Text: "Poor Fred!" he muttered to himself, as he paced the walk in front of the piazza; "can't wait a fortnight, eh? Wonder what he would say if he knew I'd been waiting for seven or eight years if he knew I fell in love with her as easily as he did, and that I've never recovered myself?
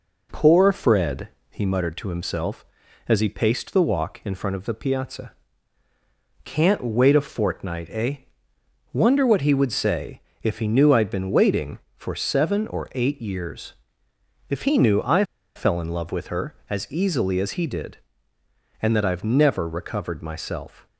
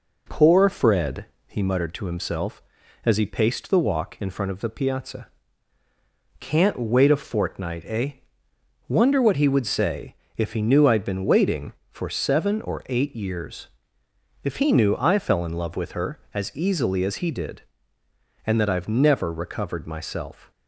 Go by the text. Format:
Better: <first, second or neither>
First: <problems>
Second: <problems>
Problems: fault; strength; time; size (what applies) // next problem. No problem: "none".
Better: second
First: pauses between "say" and "if"; slight; at 10.2 s; 0.24 s long // pauses between "years" and "if"; noticeable; at 13.7 s; 0.76 s long // pauses between "I" and "fell"; slight; at 15.2 s; 0.31 s long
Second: pauses between "say" and "if"; slight; at 10.1 s; 0.24 s long // pauses between "years" and "if"; noticeable; at 13.6 s; 0.76 s long